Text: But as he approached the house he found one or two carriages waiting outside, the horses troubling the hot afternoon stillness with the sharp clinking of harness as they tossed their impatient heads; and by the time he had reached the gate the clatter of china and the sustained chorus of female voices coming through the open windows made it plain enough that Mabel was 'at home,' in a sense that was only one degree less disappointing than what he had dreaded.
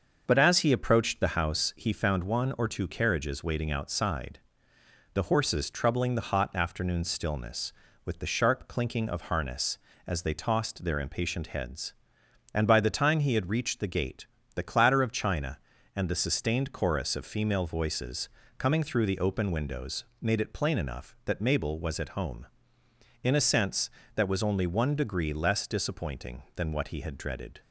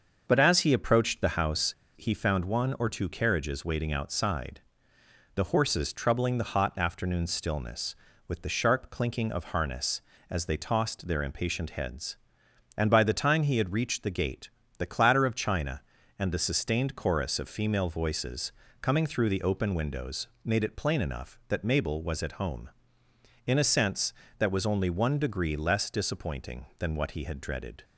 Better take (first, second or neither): first